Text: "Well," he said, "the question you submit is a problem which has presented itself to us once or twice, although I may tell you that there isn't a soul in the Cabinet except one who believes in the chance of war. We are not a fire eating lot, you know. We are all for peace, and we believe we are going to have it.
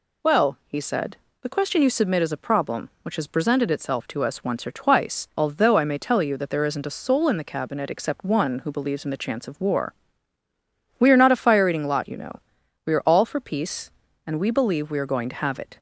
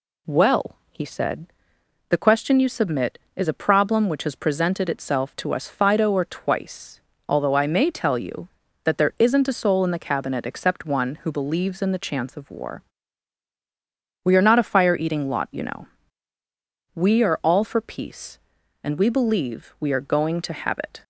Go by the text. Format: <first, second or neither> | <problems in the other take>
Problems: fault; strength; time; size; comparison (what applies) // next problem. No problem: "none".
first | says "fido" for "once"; at 5.6 s